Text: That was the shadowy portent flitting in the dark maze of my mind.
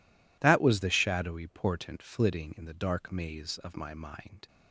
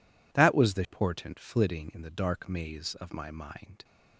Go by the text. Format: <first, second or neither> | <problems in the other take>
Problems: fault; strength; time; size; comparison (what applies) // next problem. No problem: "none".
first | skips "shadowy"; at 0.8 s